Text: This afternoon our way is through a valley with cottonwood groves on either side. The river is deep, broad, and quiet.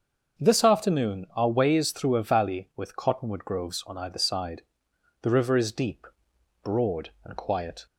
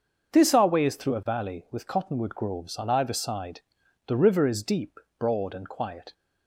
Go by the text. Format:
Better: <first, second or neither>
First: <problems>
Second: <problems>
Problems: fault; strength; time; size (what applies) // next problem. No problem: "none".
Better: first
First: starts louder than the rest; until 1.4 s; 6.5 dB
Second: starts louder than the rest; until 1.3 s; 6 dB // skips "afternoon"; at 0.5 s